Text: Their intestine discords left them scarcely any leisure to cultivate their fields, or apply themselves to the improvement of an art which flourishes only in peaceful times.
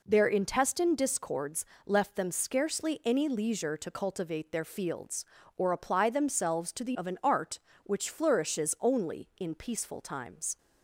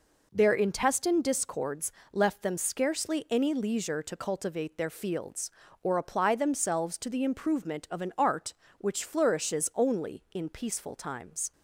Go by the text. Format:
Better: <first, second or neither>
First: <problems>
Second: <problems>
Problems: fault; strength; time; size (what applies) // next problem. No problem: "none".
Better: second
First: pauses between "discords" and "left"; slight; at 1.6 s; 0.22 s long // skips "improvement"; at 6.9 s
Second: pauses between "discords" and "left"; slight; at 1.9 s; 0.22 s long